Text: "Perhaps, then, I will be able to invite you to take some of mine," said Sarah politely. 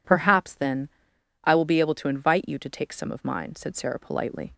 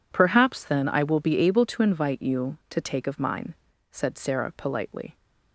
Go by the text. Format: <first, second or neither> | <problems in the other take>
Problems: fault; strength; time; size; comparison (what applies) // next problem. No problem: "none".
first | skips "some"; at 3.0 s